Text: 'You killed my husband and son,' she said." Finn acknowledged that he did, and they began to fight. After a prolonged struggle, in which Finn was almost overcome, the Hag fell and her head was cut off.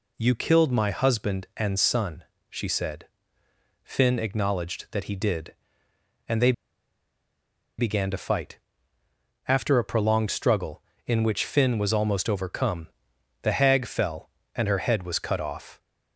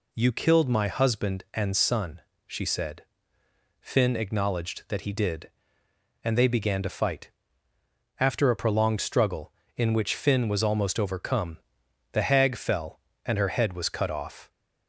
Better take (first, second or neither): second